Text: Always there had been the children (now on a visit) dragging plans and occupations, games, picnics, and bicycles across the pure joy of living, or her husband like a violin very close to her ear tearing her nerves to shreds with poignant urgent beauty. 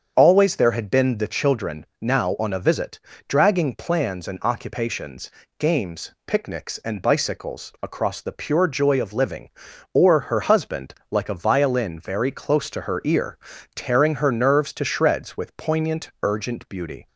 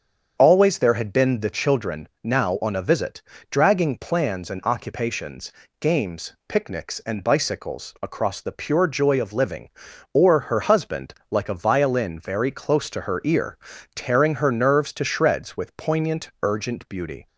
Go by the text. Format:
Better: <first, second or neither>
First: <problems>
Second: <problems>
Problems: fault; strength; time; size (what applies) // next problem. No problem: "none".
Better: neither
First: starts louder than the rest; strong; until 1.1 s; 7.5 dB // pauses between "husband" and "like"; slight; at 10.9 s; 0.16 s long // pauses between "ear" and "tearing"; at 13.3 s; 0.38 s long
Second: starts louder than the rest; until 1.4 s; 7 dB // pauses between "husband" and "like"; slight; at 11.1 s; 0.16 s long // pauses between "ear" and "tearing"; at 13.5 s; 0.38 s long